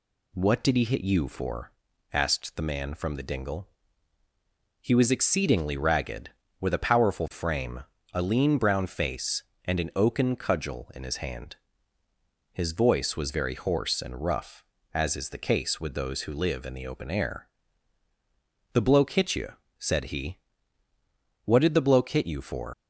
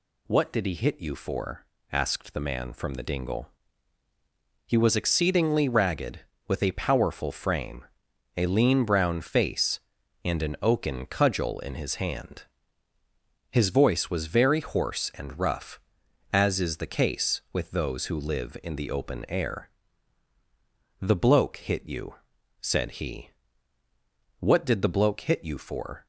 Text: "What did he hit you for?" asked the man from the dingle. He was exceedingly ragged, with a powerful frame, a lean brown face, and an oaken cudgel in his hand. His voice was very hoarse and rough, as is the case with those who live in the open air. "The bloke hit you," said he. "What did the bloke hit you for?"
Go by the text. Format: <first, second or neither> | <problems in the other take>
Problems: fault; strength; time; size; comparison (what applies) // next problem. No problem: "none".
second | leaves "for" unfinished; at 22.7 s; 115 ms